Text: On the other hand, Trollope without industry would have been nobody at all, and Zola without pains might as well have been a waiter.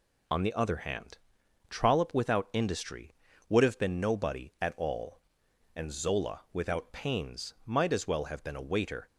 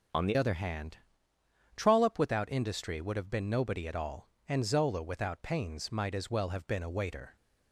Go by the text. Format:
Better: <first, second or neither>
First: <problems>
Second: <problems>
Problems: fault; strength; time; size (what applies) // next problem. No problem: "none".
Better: first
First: none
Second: changes voice at "other"; from 0.3 s on; 7.0 s long